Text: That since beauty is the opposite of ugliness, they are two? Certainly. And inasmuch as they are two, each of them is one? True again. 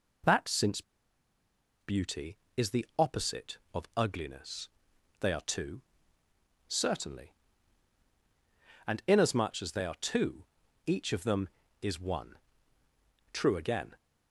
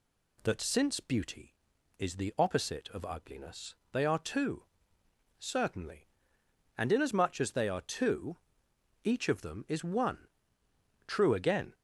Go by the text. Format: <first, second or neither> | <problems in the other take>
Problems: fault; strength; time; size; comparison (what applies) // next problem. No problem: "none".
second | pauses between "since" and "beauty"; at 0.8 s; 1.0 s long